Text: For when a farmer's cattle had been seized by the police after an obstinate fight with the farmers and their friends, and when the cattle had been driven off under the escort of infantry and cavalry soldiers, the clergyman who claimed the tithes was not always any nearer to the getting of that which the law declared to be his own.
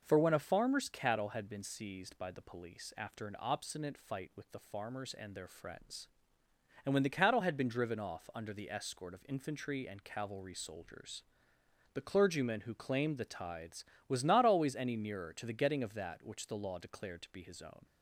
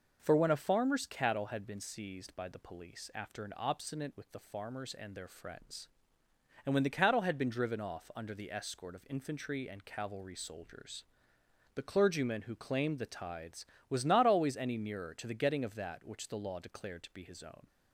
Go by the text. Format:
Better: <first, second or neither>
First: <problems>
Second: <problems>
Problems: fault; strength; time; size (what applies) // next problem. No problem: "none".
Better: first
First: none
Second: skips "fight"; at 4.1 s